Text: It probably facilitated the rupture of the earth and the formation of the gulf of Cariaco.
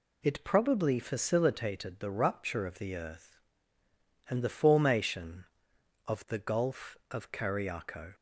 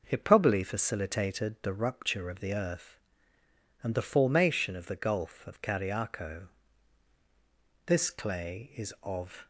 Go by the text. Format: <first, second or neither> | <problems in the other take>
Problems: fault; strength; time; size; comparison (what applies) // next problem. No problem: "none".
first | goes on to say "This clay is of"; from 7.8 s on; 1.6 s long